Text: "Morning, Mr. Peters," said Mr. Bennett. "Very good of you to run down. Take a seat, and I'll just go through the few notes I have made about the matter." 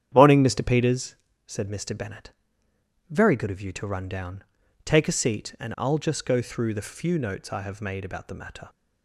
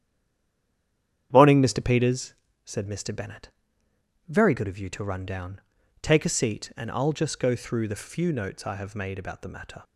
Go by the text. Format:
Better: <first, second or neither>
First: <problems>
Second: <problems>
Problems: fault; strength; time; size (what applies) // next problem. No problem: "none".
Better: first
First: starts louder than the rest; strong; until 1.1 s; 9.5 dB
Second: stays silent before the first word; noticeable; until 1.3 s; 1.3 s long // starts louder than the rest; strong; until 2.3 s; 9.5 dB